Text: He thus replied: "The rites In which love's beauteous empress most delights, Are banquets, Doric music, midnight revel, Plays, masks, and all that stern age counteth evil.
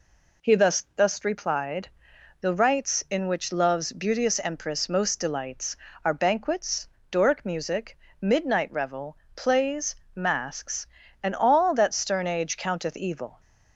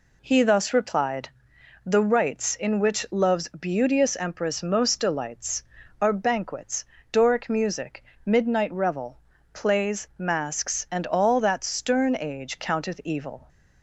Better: second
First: says "thus" twice; at 0.9 s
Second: none

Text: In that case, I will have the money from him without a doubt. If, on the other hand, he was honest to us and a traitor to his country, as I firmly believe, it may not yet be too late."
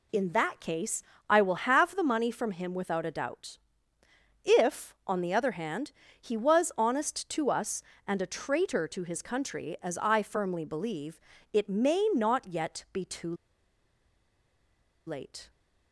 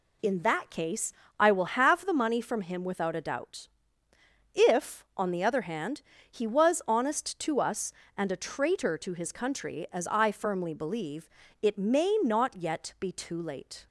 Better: second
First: pauses between "too" and "late"; strong; at 13.3 s; 1.7 s long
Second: none

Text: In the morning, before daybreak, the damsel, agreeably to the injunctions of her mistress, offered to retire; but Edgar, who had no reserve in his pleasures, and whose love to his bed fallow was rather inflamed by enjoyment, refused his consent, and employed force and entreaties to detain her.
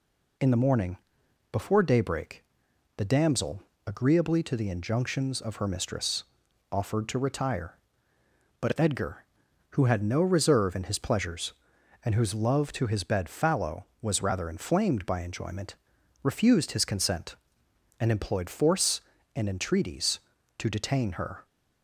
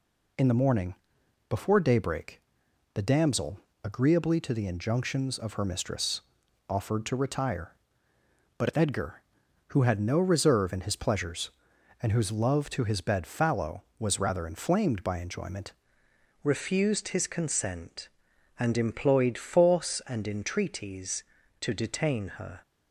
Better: first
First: none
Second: changes voice at "refused"; from 16.4 s on; 6.2 s long

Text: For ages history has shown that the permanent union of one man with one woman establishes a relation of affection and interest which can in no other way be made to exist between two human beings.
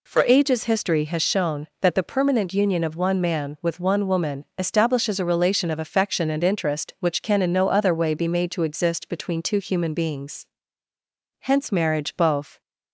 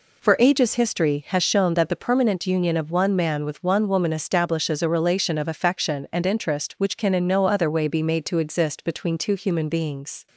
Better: second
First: goes on to say "Hence marriage both"; noticeable; from 11.4 s on; 1.2 s long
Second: none

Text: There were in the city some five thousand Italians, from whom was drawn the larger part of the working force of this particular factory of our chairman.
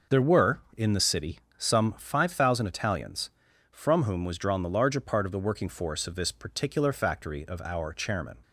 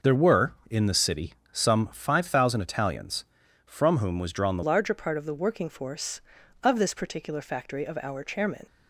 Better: first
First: pauses between "city" and "some"; slight; at 1.3 s; 0.18 s long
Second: pauses between "city" and "some"; slight; at 1.3 s; 0.18 s long // changes voice at "larger"; from 4.6 s on; 4.0 s long

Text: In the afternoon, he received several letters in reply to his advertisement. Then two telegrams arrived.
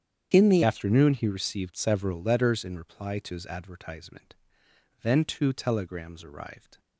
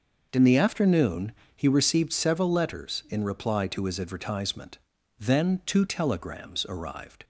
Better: second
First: starts louder than the rest; strong; until 1.3 s; 9 dB // changes voice at "afternoon"; from 0.6 s on; 6.1 s long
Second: none

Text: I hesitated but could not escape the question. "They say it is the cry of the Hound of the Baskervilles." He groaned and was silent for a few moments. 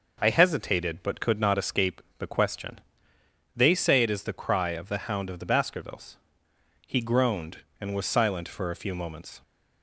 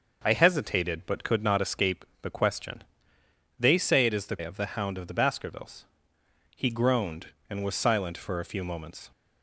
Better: first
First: pauses between "escape" and "the"; slight; at 2.0 s; 0.18 s long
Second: starts louder than the rest; noticeable; until 1.2 s; 6 dB // pauses between "escape" and "the"; slight; at 2.0 s; 0.18 s long // skips "cry"; at 4.3 s

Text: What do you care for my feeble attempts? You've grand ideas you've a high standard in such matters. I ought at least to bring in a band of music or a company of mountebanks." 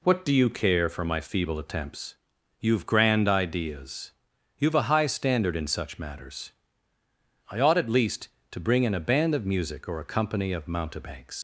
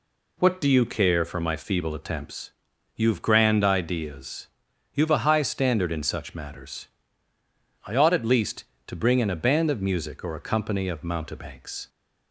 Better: second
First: pauses between "ideas" and "you've"; noticeable; at 4.1 s; 0.48 s long // leaves "mountebanks" unfinished; at 11.3 s; 105 ms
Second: pauses between "ideas" and "you've"; noticeable; at 4.4 s; 0.48 s long

